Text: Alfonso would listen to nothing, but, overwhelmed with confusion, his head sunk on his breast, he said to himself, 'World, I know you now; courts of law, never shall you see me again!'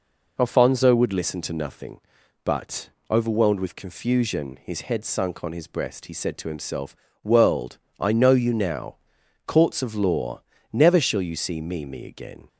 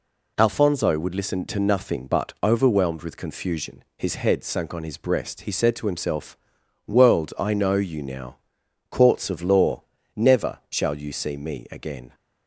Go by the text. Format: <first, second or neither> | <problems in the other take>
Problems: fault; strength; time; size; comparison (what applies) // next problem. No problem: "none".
second | says "me" twice; at 11.8 s